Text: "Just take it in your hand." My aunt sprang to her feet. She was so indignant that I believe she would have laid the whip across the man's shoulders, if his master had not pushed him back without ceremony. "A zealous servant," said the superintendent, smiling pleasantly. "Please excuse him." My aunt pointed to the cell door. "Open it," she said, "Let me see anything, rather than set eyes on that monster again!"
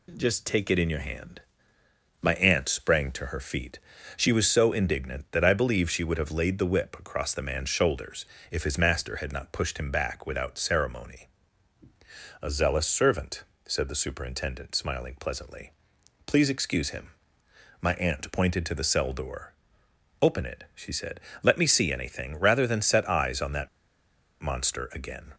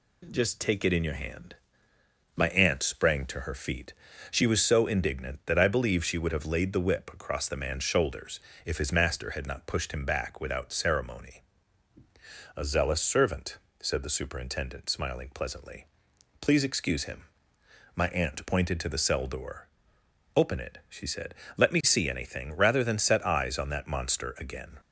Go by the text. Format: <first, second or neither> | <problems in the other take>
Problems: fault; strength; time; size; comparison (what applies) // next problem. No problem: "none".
second | pauses between "that" and "monster"; noticeable; at 23.6 s; 0.73 s long